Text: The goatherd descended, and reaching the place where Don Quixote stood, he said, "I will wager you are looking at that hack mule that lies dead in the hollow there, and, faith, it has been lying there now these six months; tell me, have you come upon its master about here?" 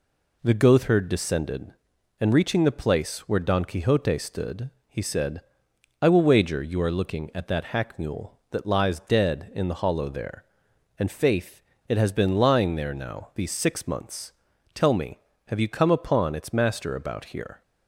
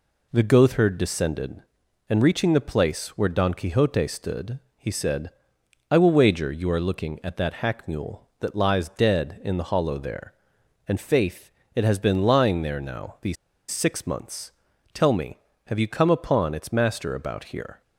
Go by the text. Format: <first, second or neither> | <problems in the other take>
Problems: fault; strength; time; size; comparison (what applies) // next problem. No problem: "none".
first | pauses between "these" and "six"; slight; at 13.3 s; 0.35 s long